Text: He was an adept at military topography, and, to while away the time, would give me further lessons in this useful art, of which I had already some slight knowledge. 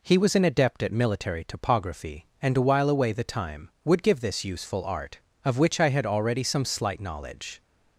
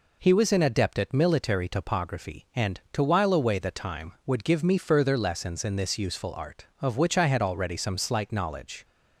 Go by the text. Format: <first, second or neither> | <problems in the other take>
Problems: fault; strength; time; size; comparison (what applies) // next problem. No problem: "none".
second | skips "me further lessons in"; at 4.2 s